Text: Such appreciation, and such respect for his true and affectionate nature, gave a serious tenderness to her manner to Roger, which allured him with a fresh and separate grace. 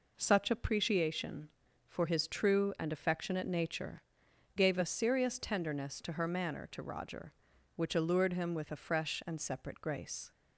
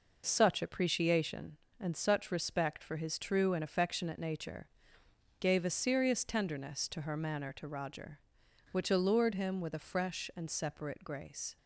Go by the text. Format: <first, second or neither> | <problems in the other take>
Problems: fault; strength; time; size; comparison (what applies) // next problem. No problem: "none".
second | skips "and such respect"; at 1.6 s